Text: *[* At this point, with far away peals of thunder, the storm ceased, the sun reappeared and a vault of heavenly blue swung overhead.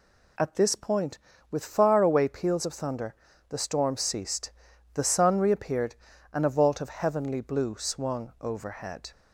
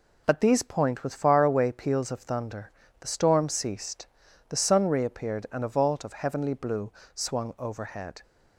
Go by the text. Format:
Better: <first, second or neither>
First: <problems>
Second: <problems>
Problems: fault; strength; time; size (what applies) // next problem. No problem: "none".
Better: first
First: none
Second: says "these" for "this"; at 0.3 s // pauses between "blue" and "swung"; slight; at 6.9 s; 0.24 s long